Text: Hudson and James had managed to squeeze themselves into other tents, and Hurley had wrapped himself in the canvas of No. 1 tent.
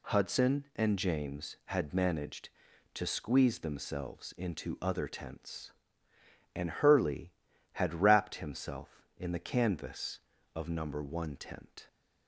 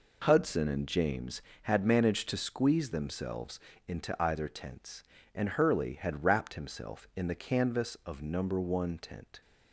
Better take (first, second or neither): first